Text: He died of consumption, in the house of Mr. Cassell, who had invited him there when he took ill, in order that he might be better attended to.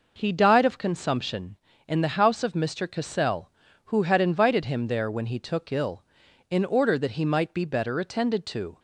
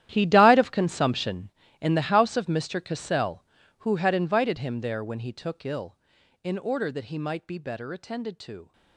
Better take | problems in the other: first | gets quieter; strong; throughout; 16.5 dB

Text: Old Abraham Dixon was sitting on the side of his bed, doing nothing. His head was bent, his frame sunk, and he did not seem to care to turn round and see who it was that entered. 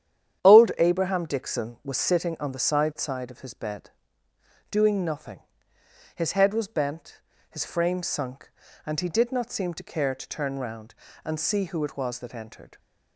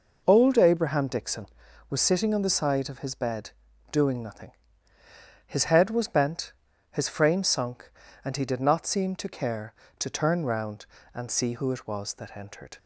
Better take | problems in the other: second | starts louder than the rest; strong; until 1.4 s; 9.5 dB // says "side" twice; at 2.9 s

